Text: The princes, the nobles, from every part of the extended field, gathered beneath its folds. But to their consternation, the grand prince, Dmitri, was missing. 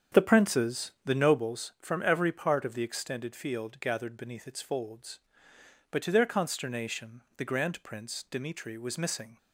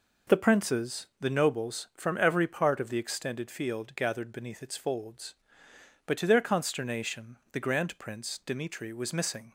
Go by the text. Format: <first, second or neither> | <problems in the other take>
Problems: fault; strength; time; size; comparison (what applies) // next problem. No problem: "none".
second | starts louder than the rest; strong; until 1.6 s; 7.5 dB